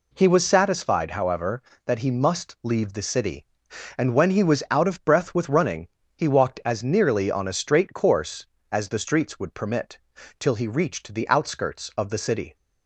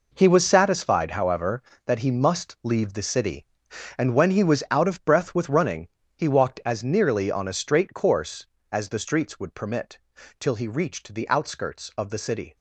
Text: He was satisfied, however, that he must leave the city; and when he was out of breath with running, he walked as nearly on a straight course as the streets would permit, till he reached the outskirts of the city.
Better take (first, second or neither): first